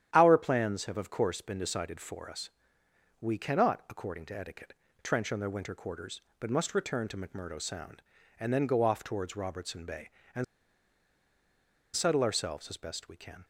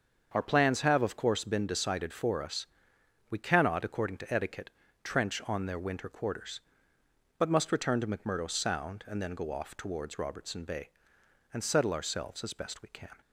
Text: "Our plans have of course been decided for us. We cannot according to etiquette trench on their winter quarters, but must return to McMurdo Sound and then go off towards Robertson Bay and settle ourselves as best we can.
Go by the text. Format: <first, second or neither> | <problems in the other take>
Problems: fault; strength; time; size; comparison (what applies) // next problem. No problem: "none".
second | starts louder than the rest; strong; until 1.1 s; 10 dB; also in the second // pauses between "etiquette" and "trench"; slight; at 4.7 s; 0.30 s long; slight in the second // pauses between "and" and "settle"; strong; at 10.4 s; 1.5 s long